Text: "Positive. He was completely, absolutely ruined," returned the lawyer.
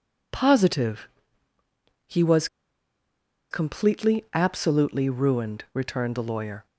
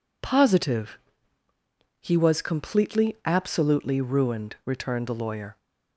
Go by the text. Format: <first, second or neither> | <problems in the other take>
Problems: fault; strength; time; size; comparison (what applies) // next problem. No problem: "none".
second | pauses between "was" and "completely"; at 2.4 s; 1.0 s long